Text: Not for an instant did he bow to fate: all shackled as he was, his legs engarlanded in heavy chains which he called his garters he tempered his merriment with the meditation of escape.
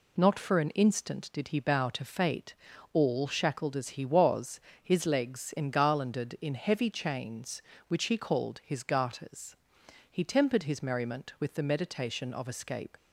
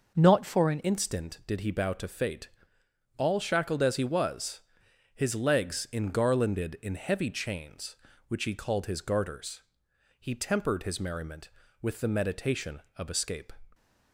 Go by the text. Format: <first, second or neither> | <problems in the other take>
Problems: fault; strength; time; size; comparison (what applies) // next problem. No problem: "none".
first | changes voice at "instant"; from 0.8 s on; 12.7 s long // pauses between "garters" and "he"; noticeable; at 9.6 s; 0.58 s long; noticeable in the first